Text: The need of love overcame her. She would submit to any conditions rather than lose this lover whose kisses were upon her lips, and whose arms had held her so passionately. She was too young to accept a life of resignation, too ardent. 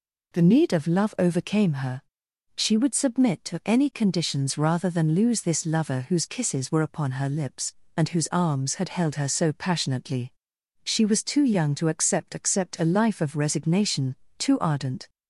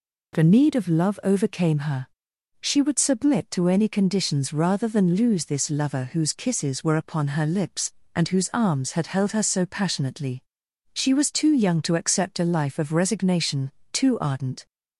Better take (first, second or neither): second